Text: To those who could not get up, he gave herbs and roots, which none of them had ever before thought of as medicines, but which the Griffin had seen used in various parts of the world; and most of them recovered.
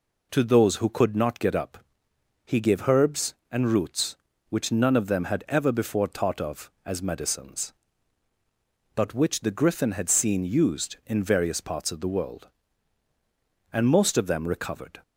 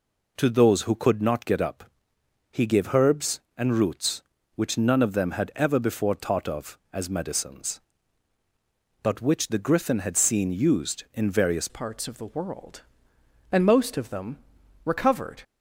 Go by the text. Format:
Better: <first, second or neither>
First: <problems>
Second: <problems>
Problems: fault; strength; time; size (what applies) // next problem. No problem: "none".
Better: first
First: none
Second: changes voice at "parts"; from 11.6 s on; 3.8 s long // pauses between "them" and "recovered"; noticeable; at 14.3 s; 0.48 s long